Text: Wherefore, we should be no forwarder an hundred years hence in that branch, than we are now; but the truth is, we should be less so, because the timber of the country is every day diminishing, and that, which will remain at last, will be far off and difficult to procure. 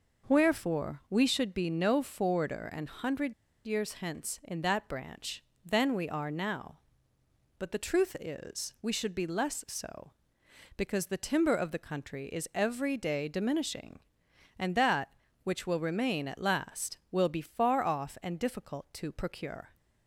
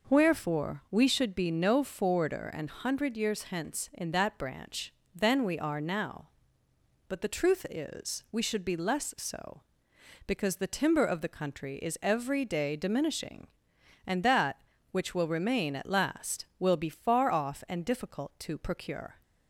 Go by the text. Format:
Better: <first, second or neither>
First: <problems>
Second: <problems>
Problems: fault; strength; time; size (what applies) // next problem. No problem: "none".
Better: second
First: pauses between "hundred" and "years"; slight; at 3.3 s; 0.34 s long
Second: none